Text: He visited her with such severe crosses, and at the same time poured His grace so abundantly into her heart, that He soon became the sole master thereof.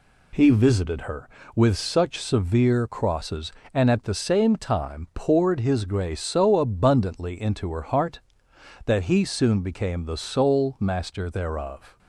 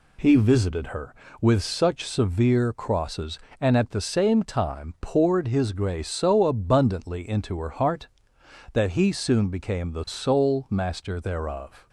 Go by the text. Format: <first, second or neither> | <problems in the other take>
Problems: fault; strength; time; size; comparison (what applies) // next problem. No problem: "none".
neither | none